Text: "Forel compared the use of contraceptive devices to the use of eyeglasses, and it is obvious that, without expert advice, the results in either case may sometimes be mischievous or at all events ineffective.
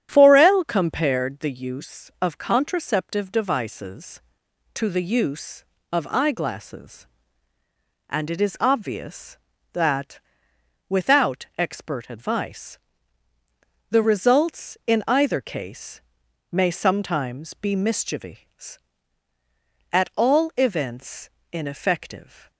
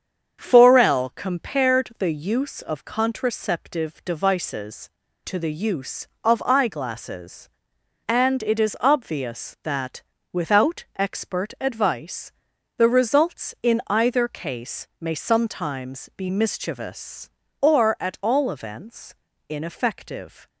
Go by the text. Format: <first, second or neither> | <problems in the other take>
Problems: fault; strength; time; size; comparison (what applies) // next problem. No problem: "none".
second | starts louder than the rest; strong; until 1.1 s; 9.5 dB; strong in the second // pauses between "case" and "may"; noticeable; at 16.0 s; 0.50 s long // skips "or"; at 19.3 s // pauses between "events" and "ineffective"; slight; at 21.2 s; 0.24 s long; slight in the second